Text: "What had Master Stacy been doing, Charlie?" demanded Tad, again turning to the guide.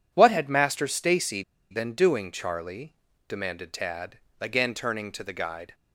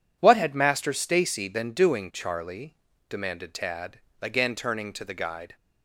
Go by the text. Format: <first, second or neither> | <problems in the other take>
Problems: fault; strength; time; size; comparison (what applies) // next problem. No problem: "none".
second | pauses between "Stacy" and "been"; slight; at 1.4 s; 0.29 s long